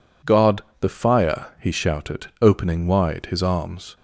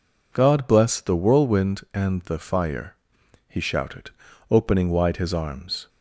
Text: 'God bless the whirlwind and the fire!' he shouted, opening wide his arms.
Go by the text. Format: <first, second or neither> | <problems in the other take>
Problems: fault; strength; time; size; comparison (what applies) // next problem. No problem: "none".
second | skips "bless the whirlwind and"; at 0.7 s